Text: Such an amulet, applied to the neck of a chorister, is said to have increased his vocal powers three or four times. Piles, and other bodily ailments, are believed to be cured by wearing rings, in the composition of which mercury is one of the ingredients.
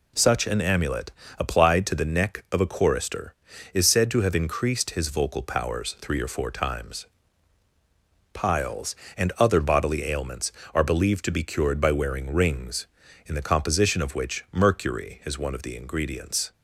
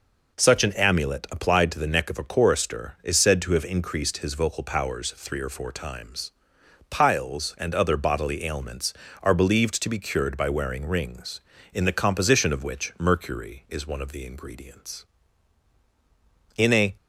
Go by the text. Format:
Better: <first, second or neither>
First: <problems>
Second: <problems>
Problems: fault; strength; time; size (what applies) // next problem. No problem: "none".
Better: first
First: none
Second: goes on to say "In a"; slight; from 16.5 s on; 0.40 s long